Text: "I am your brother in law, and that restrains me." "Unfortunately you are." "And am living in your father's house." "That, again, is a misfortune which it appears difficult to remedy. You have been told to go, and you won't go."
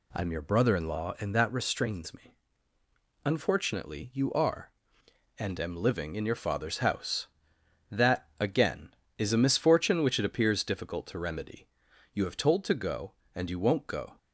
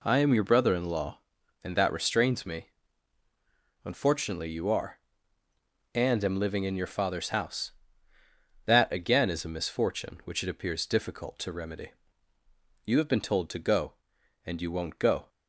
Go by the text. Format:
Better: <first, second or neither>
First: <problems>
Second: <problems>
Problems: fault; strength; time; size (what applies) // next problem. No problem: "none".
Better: second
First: skips "been"; at 12.3 s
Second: none